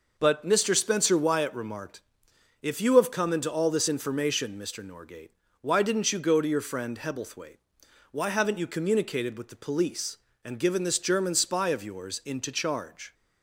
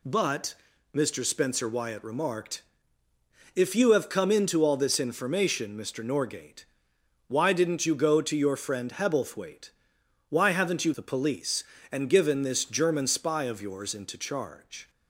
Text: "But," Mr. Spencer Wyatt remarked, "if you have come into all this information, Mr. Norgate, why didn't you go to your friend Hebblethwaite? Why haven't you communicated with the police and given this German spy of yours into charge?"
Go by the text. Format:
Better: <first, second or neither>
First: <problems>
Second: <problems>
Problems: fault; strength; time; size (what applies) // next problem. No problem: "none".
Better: first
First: none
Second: skips "communicated with"; at 10.9 s